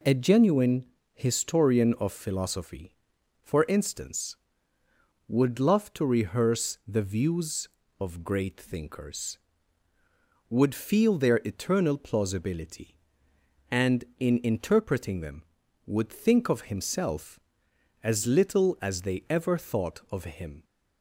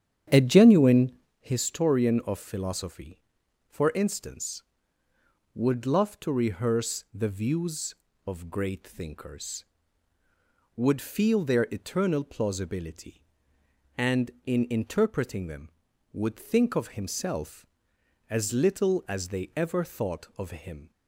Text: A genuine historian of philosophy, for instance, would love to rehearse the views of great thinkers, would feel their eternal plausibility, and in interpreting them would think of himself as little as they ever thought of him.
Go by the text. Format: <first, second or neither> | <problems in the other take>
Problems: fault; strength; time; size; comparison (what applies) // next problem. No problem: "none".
first | starts louder than the rest; strong; until 1.4 s; 9 dB // pauses between "genuine" and "historian"; slight; at 1.1 s; 0.28 s long; slight in the first